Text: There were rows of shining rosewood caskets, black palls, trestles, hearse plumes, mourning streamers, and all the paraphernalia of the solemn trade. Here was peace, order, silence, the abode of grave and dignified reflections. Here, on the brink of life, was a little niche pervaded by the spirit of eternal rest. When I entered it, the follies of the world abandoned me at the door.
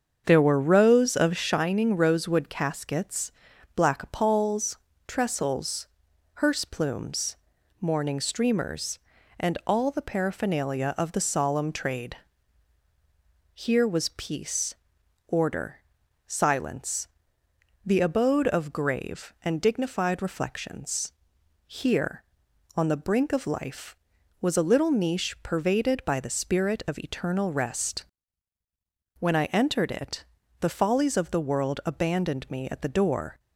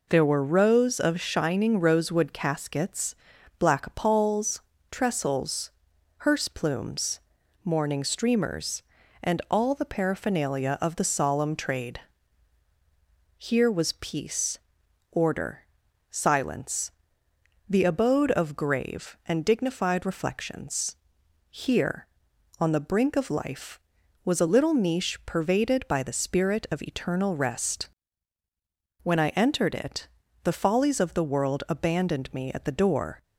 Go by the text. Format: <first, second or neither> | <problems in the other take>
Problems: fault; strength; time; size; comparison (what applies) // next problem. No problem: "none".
second | starts louder than the rest; until 1.7 s; 7 dB